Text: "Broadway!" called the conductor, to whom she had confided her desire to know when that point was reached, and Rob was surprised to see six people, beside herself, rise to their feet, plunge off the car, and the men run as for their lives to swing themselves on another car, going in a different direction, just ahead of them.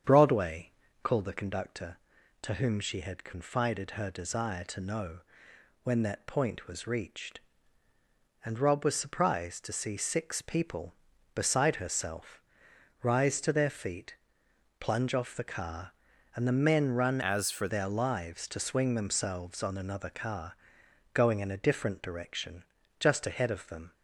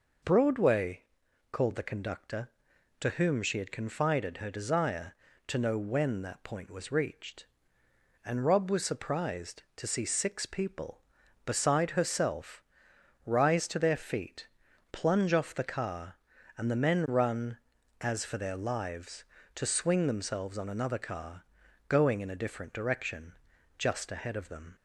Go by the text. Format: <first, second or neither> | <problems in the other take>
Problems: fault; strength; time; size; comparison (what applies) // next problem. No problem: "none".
second | starts louder than the rest; strong; until 1.3 s; 8 dB // pauses between "know" and "when"; noticeable; at 5.2 s; 0.62 s long // changes voice from "as" to "for"; from 17.2 to 17.6 s; 0.4 s long